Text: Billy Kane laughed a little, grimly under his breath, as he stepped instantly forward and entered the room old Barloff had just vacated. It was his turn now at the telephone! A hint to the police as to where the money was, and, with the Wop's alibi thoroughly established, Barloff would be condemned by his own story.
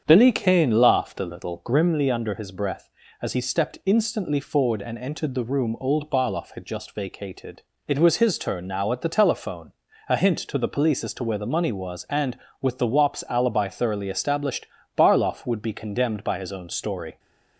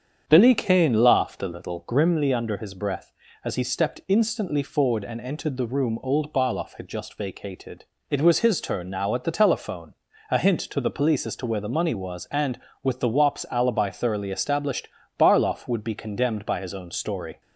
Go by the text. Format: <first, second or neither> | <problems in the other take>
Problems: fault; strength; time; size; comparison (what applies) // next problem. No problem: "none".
neither | starts louder than the rest; strong; the same in both